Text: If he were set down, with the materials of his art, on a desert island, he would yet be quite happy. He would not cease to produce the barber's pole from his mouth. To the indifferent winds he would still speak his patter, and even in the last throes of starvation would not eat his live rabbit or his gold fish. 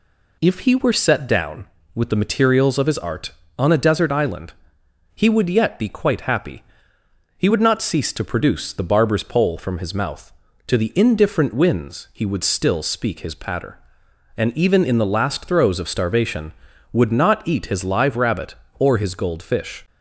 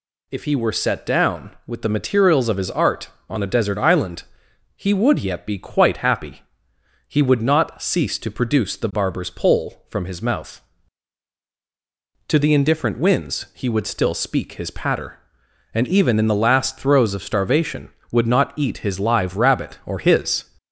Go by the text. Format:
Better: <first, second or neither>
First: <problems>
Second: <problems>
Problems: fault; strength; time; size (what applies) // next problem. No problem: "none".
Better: first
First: none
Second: stops before "gold fish"; at 20.5 s